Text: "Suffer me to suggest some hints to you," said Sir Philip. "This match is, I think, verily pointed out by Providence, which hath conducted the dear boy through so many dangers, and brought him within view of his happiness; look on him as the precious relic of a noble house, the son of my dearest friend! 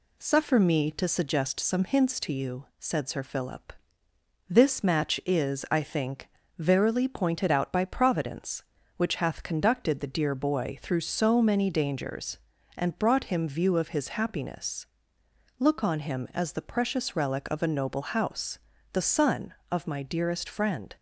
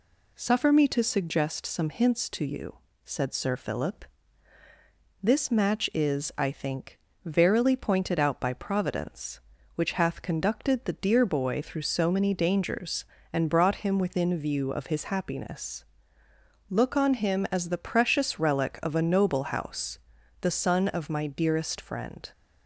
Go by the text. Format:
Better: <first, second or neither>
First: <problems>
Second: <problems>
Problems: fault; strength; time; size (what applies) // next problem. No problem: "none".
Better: second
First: skips "within"; at 13.4 s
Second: none